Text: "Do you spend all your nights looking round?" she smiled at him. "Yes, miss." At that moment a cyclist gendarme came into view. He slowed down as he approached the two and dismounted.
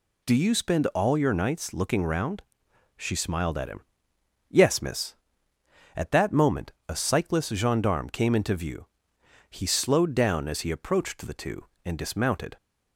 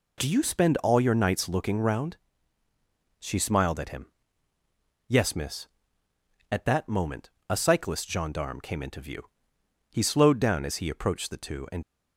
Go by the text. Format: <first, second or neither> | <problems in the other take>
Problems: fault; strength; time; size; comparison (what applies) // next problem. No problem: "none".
first | pauses between "moment" and "a"; slight; at 7.2 s; 0.20 s long; slight in the first // stops before "dismounted"; at 11.8 s